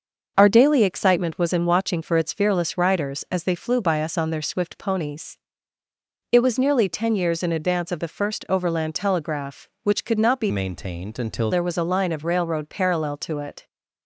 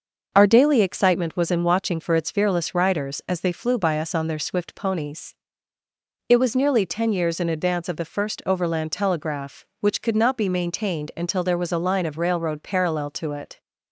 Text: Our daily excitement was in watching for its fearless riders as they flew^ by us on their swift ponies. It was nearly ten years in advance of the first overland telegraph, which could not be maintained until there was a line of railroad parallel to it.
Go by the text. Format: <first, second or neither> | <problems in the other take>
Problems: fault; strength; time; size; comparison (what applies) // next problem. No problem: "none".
second | starts louder than the rest; noticeable; until 1.3 s; 6 dB; noticeable in the second // changes voice from "maintained" to "until"; from 10.4 to 11.4 s; 1.0 s long